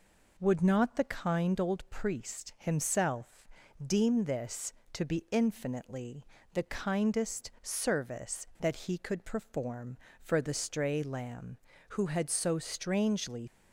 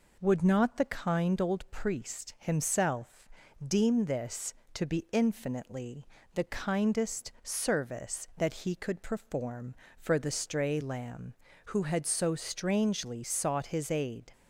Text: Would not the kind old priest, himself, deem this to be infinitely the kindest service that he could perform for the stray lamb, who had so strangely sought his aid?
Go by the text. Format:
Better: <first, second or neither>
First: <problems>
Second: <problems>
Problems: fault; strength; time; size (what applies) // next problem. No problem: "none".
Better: second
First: pauses between "infinitely" and "the"; slight; at 6.2 s; 0.26 s long // stops before "sought his aid"; at 13.4 s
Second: pauses between "infinitely" and "the"; slight; at 6.0 s; 0.26 s long